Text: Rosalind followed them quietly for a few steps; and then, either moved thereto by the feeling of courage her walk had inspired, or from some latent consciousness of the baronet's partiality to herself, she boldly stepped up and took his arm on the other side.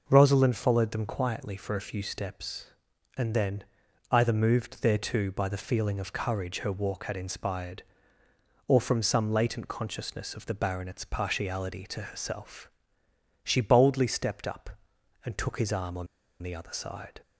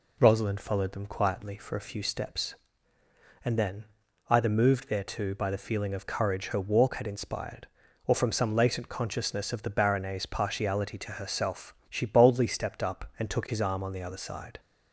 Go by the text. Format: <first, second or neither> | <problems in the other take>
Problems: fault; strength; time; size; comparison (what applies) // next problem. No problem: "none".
second | pauses between "on" and "the"; slight; at 16.0 s; 0.35 s long